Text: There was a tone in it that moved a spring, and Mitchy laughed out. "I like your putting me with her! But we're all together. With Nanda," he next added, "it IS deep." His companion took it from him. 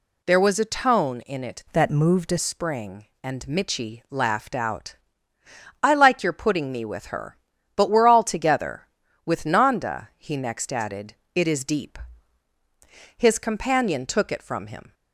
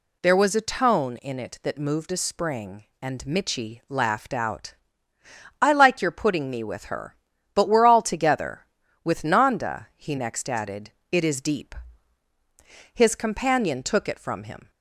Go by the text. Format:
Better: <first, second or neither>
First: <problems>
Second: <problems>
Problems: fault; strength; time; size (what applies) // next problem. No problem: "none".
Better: second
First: changes voice from "that" to "a"; from 1.7 to 2.3 s; 0.6 s long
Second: none